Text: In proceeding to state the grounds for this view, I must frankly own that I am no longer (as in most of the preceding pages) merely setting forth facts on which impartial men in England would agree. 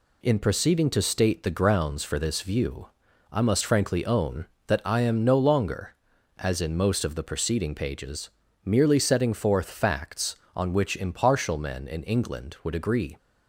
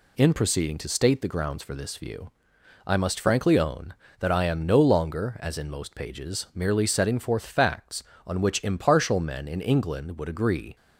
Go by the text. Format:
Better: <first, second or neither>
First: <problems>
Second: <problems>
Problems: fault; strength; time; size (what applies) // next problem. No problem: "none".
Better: first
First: none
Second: skips "of the preceding"; at 5.9 s